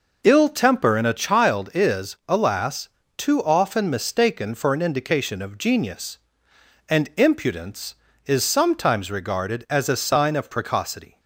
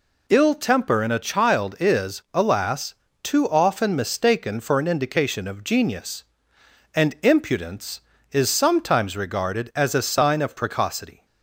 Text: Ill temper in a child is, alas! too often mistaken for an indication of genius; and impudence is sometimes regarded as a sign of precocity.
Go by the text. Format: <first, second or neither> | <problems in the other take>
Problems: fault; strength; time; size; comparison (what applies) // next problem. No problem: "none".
second | starts louder than the rest; noticeable; until 1.6 s; 5 dB